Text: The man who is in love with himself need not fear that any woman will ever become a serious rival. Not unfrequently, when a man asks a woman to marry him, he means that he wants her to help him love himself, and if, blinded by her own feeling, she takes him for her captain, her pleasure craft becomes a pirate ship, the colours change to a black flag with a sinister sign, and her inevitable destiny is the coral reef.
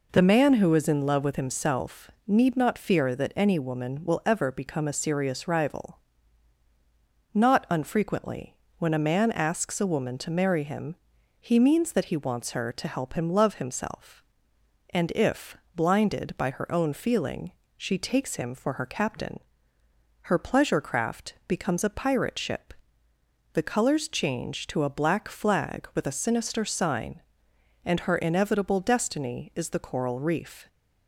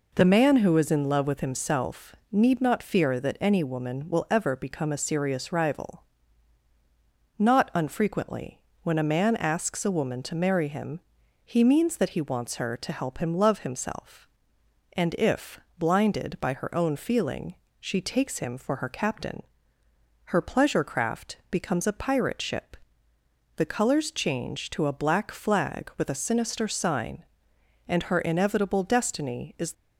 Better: first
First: pauses between "himself" and "need"; slight; at 2.0 s; 0.16 s long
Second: pauses between "himself" and "need"; slight; at 2.1 s; 0.16 s long // stops before "the coral reef"; at 29.7 s

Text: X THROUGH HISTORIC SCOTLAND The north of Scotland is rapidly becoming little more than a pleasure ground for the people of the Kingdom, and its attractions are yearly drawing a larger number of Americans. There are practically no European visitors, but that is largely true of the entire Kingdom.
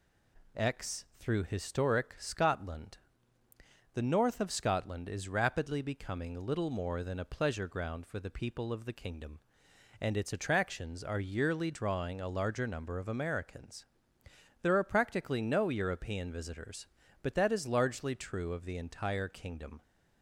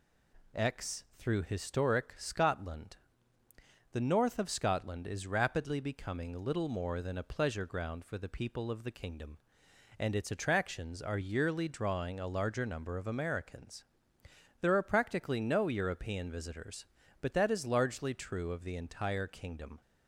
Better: neither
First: pauses between "SCOTLAND" and "The"; noticeable; at 2.9 s; 0.96 s long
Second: pauses between "SCOTLAND" and "The"; noticeable; at 2.9 s; 0.95 s long

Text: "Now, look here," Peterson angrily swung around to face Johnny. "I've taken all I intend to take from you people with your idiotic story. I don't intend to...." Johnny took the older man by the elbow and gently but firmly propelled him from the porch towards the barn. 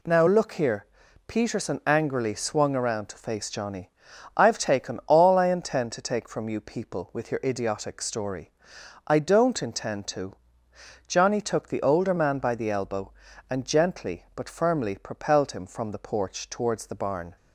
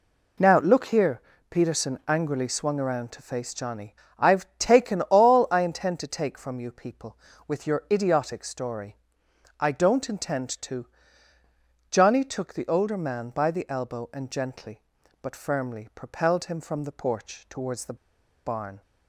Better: first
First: none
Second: pauses between "the" and "barn"; noticeable; at 17.9 s; 0.48 s long

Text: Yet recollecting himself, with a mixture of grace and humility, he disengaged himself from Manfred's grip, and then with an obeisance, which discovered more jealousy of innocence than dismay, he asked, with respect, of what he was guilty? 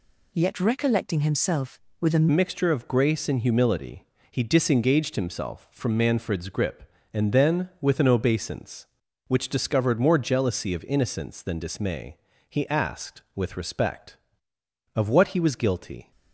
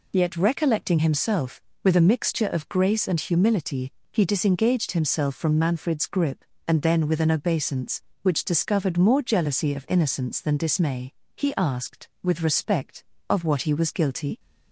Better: second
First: changes voice at "mixture"; from 2.3 s on; 13.8 s long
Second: none

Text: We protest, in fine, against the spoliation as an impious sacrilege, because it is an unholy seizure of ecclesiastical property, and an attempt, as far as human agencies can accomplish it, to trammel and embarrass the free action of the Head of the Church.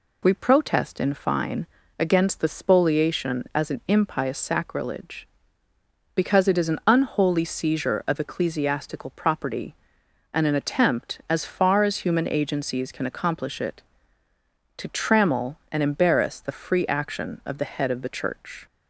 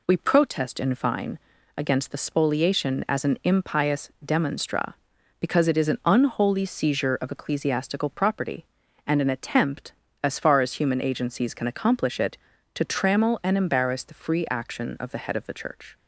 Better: first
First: none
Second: says "demonstra" for "sacrilege"; at 4.2 s

